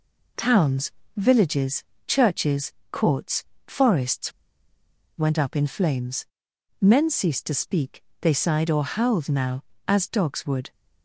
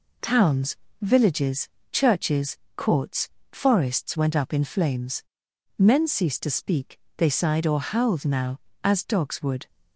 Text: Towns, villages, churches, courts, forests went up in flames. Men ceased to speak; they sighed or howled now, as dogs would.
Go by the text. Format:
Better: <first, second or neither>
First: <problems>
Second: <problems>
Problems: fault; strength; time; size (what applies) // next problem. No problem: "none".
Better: second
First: pauses between "forests" and "went"; noticeable; at 4.3 s; 0.86 s long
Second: none